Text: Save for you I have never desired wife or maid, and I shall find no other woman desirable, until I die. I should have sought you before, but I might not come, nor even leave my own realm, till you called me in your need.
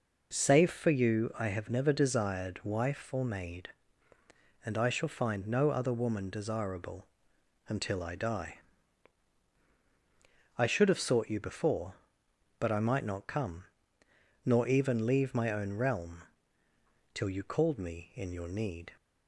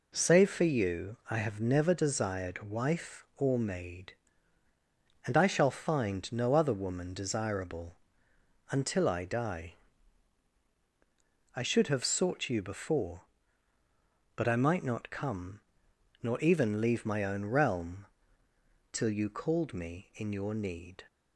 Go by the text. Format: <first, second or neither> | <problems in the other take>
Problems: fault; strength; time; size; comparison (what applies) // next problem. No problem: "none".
neither | none